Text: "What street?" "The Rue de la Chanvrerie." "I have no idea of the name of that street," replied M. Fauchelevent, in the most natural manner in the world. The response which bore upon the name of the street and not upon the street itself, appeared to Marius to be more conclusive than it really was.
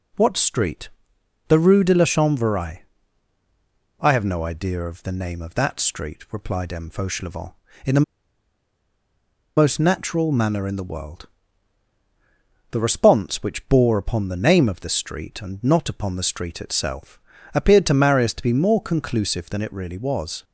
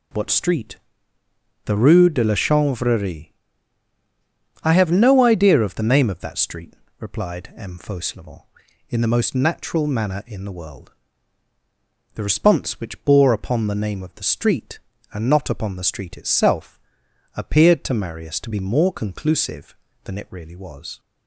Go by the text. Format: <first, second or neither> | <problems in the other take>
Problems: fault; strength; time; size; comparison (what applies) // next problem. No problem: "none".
second | pauses between "the" and "most"; strong; at 8.0 s; 1.5 s long